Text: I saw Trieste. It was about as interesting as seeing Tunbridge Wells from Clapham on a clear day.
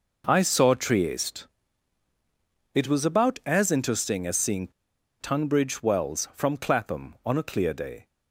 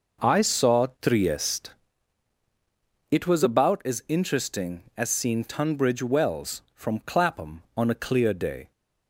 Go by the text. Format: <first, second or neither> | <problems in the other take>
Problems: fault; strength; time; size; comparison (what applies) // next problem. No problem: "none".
second | pauses between "seeing" and "Tunbridge"; noticeable; at 4.6 s; 0.51 s long